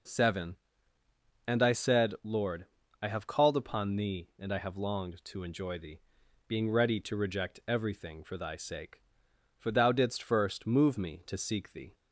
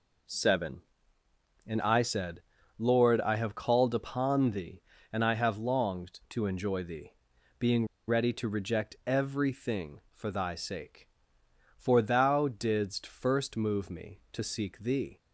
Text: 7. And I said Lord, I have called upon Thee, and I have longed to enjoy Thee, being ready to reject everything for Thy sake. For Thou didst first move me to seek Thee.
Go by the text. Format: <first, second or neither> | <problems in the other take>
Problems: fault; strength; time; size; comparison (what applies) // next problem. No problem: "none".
first | pauses between "said" and "Lord"; at 2.4 s; 0.38 s long // pauses between "being" and "ready"; slight; at 7.8 s; 0.22 s long